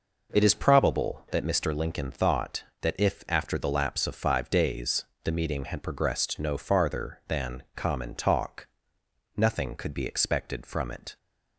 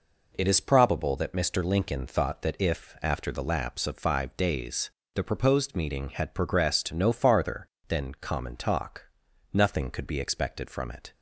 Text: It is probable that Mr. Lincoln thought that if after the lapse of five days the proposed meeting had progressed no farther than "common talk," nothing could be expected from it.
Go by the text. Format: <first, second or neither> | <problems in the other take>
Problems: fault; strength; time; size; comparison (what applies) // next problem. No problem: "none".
second | pauses between "days" and "the"; slight; at 5.0 s; 0.22 s long; slight in the second // skips "proposed"; at 5.3 s